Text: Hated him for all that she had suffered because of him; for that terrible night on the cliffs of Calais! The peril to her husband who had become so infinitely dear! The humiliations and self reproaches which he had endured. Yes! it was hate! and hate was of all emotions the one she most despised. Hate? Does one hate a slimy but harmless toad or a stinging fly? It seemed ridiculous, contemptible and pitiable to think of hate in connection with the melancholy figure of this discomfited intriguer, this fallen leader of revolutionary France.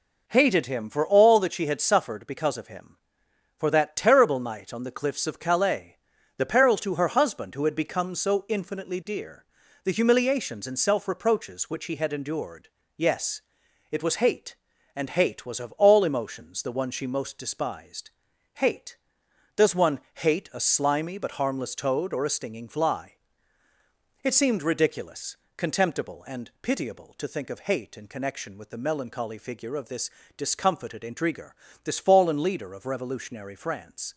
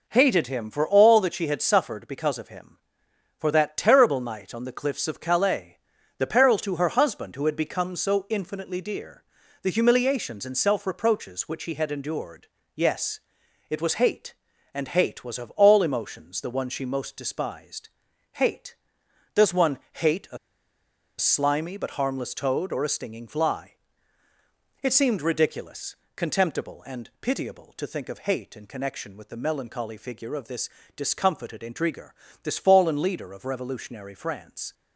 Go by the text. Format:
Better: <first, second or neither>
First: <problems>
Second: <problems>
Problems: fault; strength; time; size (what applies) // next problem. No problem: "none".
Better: first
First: pauses between "this" and "discomfited"; slight; at 30.1 s; 0.26 s long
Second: pauses between "a" and "slimy"; noticeable; at 20.3 s; 0.81 s long // pauses between "this" and "discomfited"; slight; at 30.6 s; 0.26 s long